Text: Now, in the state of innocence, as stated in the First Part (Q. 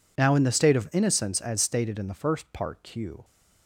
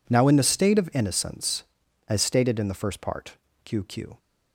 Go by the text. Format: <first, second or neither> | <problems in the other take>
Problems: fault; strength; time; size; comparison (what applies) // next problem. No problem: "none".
first | says "Q" twice; at 3.8 s